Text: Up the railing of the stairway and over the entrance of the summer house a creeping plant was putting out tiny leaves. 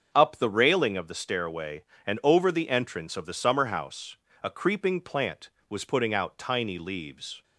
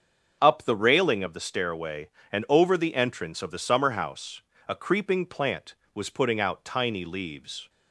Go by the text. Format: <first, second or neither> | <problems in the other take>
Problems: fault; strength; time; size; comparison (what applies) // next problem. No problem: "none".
neither | starts louder than the rest; the same in both // pauses between "house" and "a"; slight; the same in both